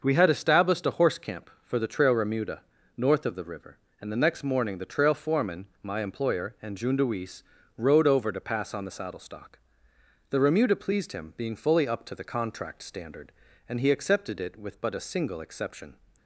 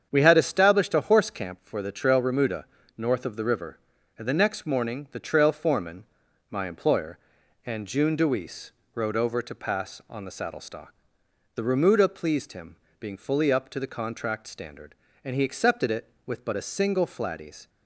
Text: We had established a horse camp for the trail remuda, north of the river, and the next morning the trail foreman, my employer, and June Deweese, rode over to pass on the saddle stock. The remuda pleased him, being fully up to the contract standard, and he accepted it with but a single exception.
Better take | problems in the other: first | starts louder than the rest; strong; until 1.1 s; 7.5 dB; also in the first // says "flatties" for "exception"; at 17.0 s

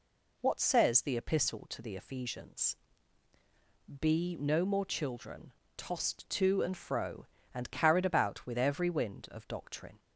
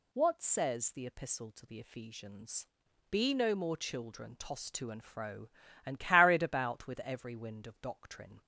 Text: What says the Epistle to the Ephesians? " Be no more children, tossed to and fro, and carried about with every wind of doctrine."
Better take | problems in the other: neither | none

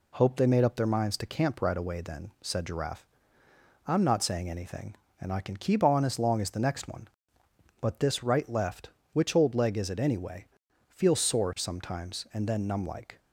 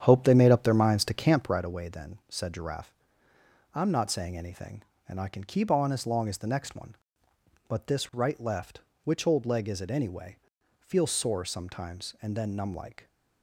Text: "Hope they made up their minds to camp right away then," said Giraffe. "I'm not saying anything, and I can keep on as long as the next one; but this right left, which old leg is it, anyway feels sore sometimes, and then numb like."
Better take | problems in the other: first | starts louder than the rest; strong; until 1.6 s; 9 dB // pauses between "anyway" and "feels"; at 10.3 s; 0.42 s long; also in the first

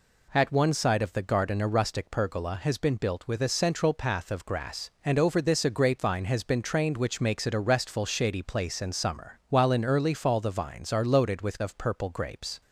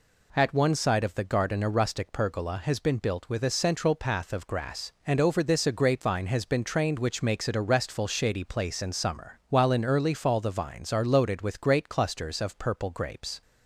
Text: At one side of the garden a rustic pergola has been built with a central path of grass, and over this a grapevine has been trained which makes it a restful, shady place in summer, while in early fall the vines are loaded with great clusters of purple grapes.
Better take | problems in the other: second | skips "great clusters"; at 11.6 s

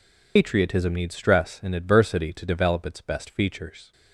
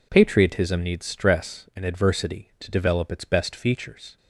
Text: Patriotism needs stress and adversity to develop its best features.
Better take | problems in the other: second | loses the start of "Patriotism"; at 0.3 s; 95 ms

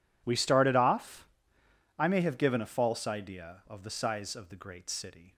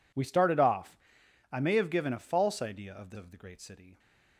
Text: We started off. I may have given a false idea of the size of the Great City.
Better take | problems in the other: first | skips "size"; at 3.1 s

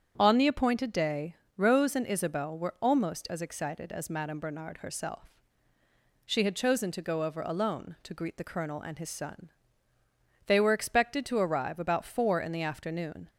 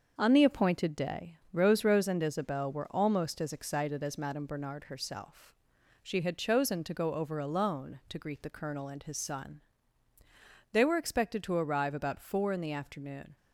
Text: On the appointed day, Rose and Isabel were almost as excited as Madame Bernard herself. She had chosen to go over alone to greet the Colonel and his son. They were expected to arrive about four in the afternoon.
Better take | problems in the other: first | starts louder than the rest; until 1.1 s; 6.5 dB; also in the first // says "Rose" twice; at 1.8 s

